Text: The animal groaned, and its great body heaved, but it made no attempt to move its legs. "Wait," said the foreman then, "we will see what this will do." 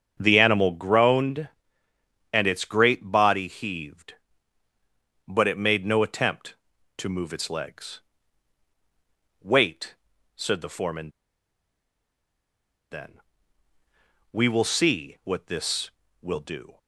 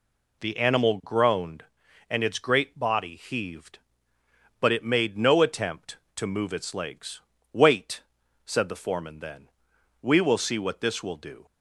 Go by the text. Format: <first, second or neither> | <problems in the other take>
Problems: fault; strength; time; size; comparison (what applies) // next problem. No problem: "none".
second | starts louder than the rest; strong; until 1.2 s; 7.5 dB // pauses between "foreman" and "then"; strong; at 11.1 s; 1.8 s long